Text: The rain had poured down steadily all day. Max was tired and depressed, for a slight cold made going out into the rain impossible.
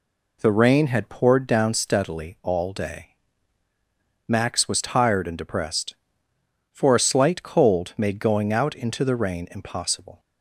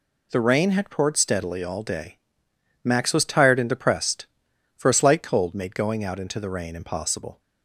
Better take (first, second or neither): first